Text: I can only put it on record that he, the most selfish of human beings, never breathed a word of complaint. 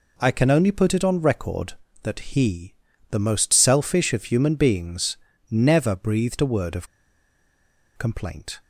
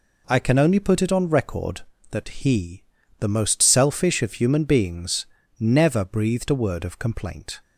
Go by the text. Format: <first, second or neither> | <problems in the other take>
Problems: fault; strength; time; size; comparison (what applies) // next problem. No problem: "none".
second | pauses between "of" and "complaint"; at 6.8 s; 1.1 s long